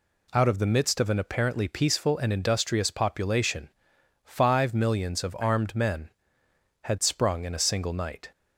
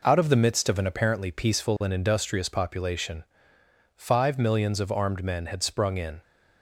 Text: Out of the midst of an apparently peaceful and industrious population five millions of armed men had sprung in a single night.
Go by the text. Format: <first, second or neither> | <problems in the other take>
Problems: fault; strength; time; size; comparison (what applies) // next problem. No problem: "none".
first | pauses between "population" and "five"; noticeable; at 3.2 s; 0.72 s long; noticeable in the first // stops before "a single night"; at 6.2 s